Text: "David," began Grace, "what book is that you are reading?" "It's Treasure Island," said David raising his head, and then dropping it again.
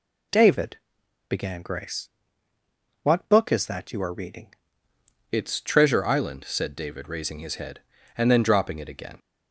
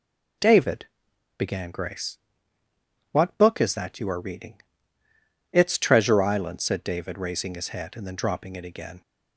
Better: second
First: changes voice at "It's"; from 5.3 s on; 3.8 s long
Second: none

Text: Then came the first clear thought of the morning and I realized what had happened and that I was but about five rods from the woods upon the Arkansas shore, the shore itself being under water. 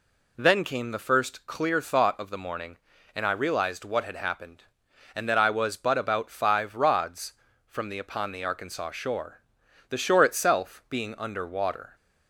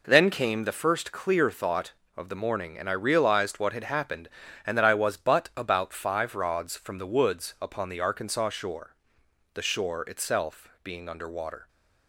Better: second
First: skips "woods"; at 7.9 s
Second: none

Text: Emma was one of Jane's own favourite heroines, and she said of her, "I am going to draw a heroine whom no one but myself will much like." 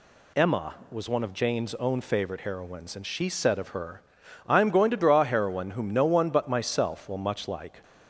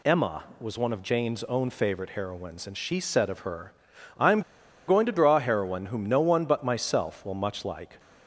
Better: first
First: none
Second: pauses between "am" and "going"; noticeable; at 4.4 s; 0.47 s long

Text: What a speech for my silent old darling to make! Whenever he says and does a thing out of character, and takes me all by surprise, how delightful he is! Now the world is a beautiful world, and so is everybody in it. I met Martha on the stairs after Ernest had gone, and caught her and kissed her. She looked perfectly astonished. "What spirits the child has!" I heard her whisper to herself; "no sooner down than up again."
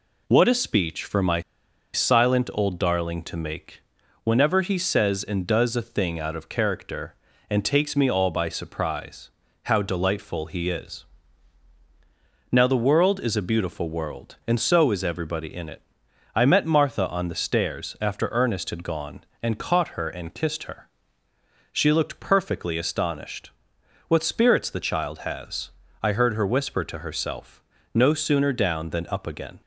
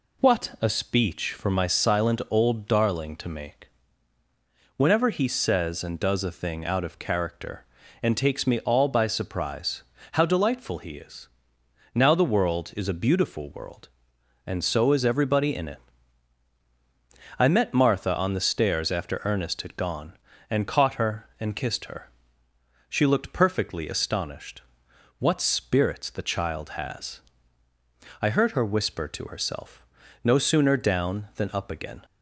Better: second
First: pauses between "my" and "silent"; noticeable; at 1.3 s; 0.54 s long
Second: none

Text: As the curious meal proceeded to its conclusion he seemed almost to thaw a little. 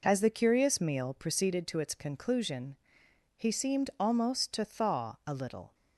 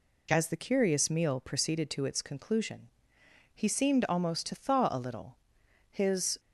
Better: first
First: pauses between "conclusion" and "he"; noticeable; at 2.7 s; 0.60 s long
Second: pauses between "conclusion" and "he"; noticeable; at 2.8 s; 0.64 s long // goes on to say "His"; from 5.8 s on; 0.50 s long

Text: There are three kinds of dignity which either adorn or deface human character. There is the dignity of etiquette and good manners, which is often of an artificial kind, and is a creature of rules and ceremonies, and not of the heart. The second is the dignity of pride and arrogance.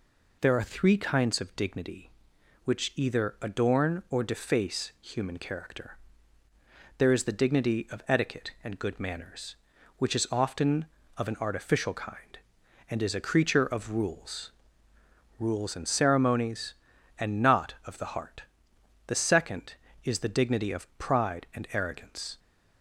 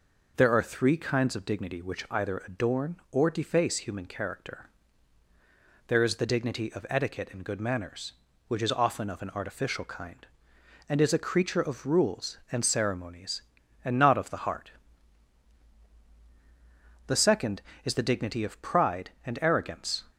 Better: second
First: says "rules" twice; at 15.3 s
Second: none

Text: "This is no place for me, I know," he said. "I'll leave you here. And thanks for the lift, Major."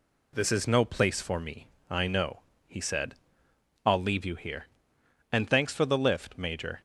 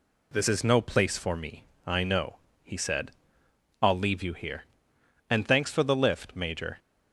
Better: neither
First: none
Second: none

